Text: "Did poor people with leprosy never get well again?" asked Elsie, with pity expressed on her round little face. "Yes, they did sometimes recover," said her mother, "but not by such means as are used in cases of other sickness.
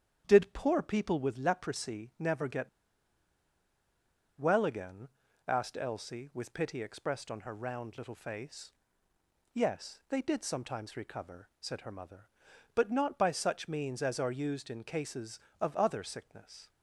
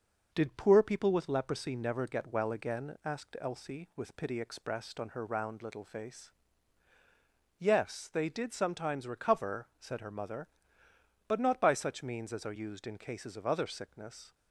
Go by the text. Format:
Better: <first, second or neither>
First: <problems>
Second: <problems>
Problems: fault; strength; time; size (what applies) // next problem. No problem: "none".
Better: second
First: starts louder than the rest; strong; until 1.2 s; 8.5 dB // pauses between "get" and "well"; strong; at 2.6 s; 1.7 s long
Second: none